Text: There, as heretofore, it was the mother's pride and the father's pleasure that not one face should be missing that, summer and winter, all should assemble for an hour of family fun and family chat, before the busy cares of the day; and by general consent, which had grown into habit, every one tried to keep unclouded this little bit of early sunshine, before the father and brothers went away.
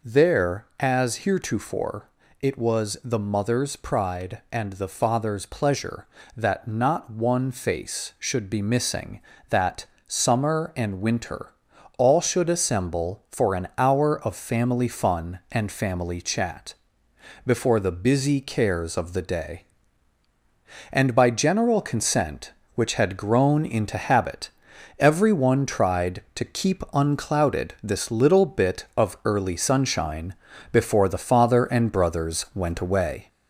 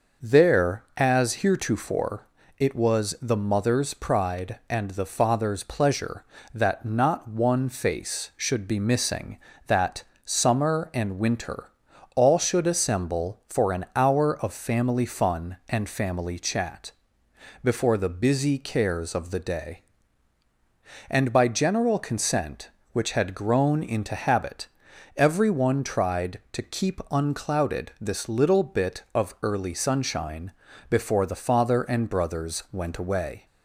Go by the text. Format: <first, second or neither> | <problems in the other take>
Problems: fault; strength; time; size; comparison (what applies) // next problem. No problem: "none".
second | gets louder; throughout; 3.5 dB